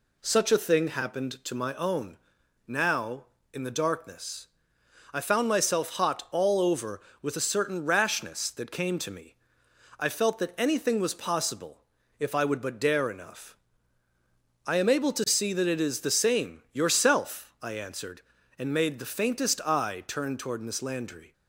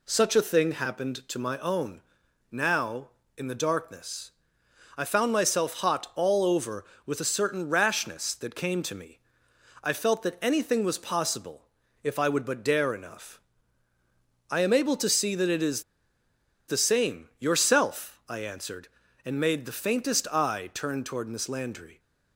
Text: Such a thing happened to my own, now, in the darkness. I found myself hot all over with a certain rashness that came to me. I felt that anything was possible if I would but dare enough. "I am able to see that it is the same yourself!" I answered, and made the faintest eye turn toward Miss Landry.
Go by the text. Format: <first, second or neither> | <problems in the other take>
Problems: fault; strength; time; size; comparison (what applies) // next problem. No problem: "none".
first | pauses between "possible" and "if"; at 11.6 s; 0.40 s long; also in the first // pauses between "is" and "the"; noticeable; at 15.8 s; 0.85 s long